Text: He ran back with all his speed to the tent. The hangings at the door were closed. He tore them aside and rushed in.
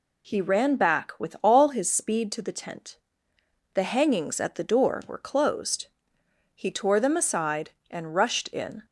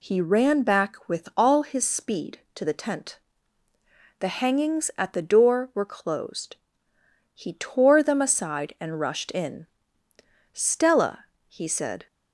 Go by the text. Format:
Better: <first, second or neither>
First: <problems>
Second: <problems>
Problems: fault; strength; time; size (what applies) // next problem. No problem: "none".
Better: first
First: none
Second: goes on to say "Stella he said"; from 10.5 s on; 1.5 s long